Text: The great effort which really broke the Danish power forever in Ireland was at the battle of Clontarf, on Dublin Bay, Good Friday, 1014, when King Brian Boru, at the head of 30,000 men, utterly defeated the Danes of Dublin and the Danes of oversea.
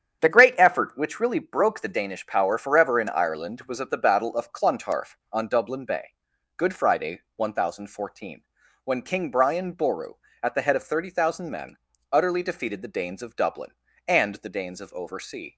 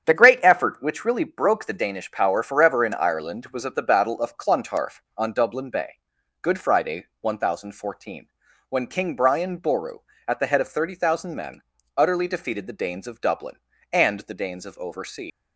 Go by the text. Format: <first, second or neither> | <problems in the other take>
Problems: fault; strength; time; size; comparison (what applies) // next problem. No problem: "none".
first | starts louder than the rest; strong; until 1.1 s; 8.5 dB; strong in the first // leaves "oversea" unfinished; at 15.3 s; 105 ms